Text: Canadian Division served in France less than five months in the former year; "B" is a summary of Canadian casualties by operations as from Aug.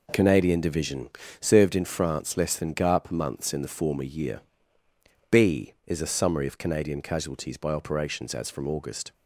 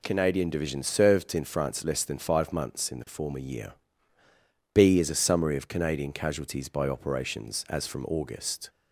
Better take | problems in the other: second | pauses between "Division" and "served"; slight; at 1.0 s; 0.30 s long // says "garp" for "five"; at 2.7 s

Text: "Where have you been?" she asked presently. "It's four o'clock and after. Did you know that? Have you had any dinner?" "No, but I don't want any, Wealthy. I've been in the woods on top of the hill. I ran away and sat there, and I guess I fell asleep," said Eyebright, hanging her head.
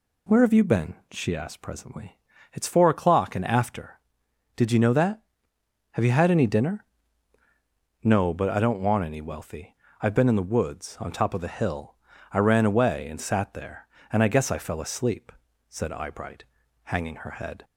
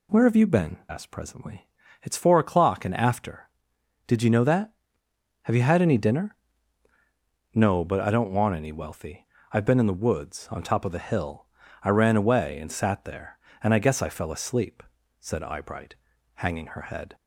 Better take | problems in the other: first | skips "she"; at 0.8 s

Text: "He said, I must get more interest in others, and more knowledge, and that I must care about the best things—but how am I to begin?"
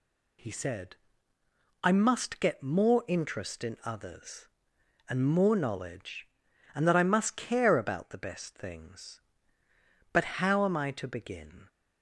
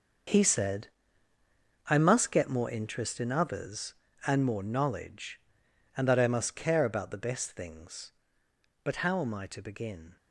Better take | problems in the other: first | gets quieter; strong; throughout; 12.5 dB

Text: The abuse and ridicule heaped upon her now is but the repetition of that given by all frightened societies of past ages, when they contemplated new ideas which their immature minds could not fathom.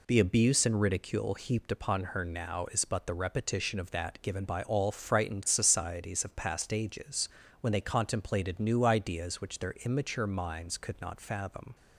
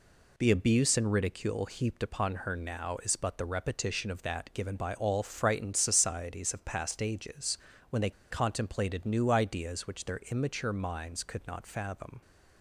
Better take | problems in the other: first | pauses between "they" and "contemplated"; slight; at 8.0 s; 0.19 s long

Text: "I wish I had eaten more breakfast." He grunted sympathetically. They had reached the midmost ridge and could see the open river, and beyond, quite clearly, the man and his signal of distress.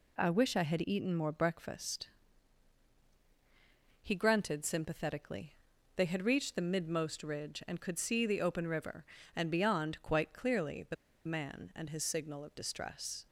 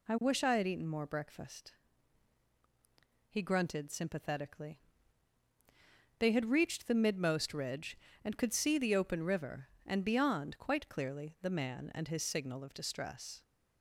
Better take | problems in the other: second | pauses between "the" and "man"; slight; at 10.9 s; 0.31 s long

